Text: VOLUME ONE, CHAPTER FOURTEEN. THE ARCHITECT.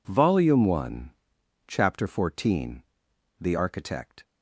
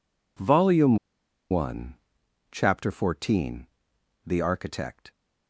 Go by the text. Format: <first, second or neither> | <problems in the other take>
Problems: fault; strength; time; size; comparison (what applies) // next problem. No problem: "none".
first | pauses between "VOLUME" and "ONE"; noticeable; at 0.9 s; 0.53 s long